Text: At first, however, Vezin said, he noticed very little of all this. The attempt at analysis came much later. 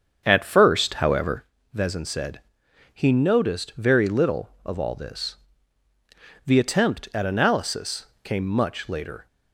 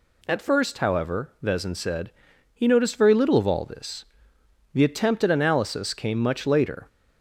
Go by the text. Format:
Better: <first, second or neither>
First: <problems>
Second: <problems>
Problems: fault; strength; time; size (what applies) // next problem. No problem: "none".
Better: second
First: starts louder than the rest; strong; until 1.5 s; 7 dB // pauses between "analysis" and "came"; slight; at 8.0 s; 0.16 s long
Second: none